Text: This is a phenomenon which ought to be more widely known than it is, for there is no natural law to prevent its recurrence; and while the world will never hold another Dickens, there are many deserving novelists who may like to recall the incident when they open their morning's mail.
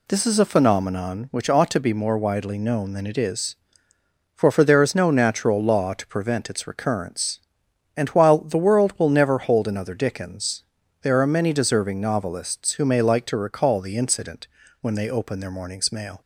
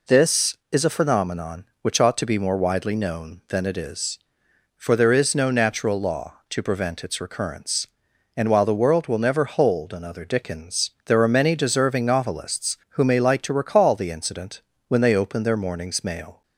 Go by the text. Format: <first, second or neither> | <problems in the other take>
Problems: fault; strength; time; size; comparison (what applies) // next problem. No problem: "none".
second | says "for" twice; at 4.5 s // pauses between "incident" and "when"; slight; at 14.4 s; 0.36 s long; slight in the second